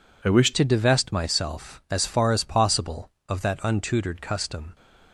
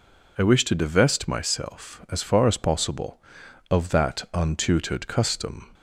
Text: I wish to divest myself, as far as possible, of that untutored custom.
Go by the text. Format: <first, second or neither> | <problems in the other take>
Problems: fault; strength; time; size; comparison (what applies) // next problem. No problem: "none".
second | changes voice at "to"; from 0.5 s on; 4.2 s long